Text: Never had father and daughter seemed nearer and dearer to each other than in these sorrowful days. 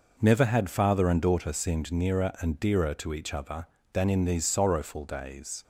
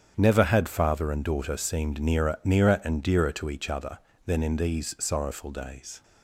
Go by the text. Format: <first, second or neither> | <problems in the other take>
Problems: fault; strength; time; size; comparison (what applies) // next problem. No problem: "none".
first | starts louder than the rest; strong; until 1.1 s; 8.5 dB // says "nearer" twice; at 2.4 s